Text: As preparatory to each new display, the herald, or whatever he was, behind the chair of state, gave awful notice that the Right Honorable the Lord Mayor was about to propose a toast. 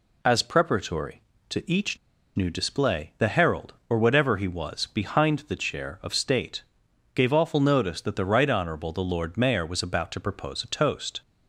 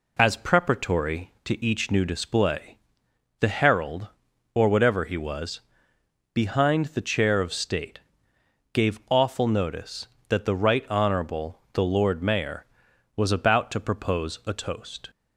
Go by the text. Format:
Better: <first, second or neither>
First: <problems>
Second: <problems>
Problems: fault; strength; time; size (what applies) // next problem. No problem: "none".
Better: second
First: pauses between "each" and "new"; at 1.9 s; 0.38 s long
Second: none